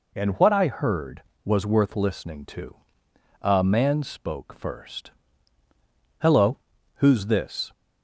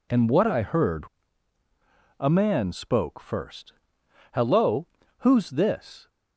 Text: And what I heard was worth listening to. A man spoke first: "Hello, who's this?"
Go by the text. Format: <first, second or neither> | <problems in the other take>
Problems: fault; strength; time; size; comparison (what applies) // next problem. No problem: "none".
first | skips "was worth listening to"; at 1.6 s